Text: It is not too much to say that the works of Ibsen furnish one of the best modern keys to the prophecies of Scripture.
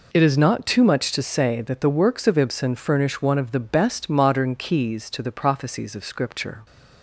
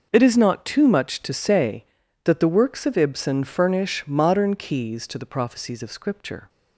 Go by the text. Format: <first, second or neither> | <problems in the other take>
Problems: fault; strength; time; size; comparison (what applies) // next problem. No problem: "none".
first | skips "one of the best"; at 4.0 s